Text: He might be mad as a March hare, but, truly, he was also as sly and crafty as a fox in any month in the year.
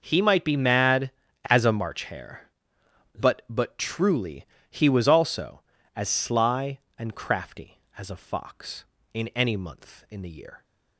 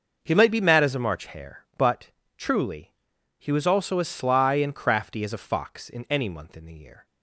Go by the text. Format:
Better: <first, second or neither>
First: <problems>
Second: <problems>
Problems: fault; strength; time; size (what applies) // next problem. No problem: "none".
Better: second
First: starts louder than the rest; noticeable; until 1.0 s; 6 dB // says "but" twice; at 3.4 s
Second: none